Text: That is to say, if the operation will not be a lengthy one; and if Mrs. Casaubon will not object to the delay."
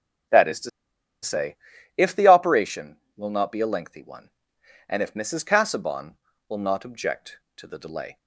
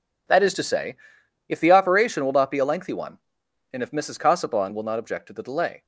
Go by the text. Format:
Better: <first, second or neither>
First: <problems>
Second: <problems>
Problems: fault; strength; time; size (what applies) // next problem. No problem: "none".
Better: second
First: pauses between "to" and "say"; noticeable; at 0.6 s; 0.52 s long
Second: none